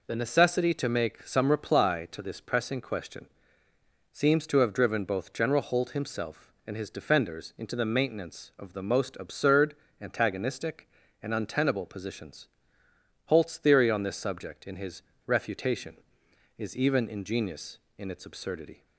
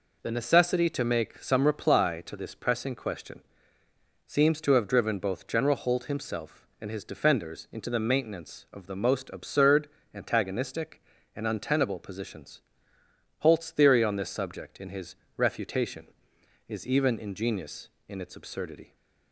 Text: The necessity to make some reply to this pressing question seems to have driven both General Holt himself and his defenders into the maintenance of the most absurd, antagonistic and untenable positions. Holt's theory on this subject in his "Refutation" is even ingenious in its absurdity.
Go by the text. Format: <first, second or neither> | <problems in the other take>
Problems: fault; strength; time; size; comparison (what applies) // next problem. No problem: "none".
neither | pauses between "question" and "seems"; noticeable; the same in both // pauses between "his" and "Refutation"; slight; the same in both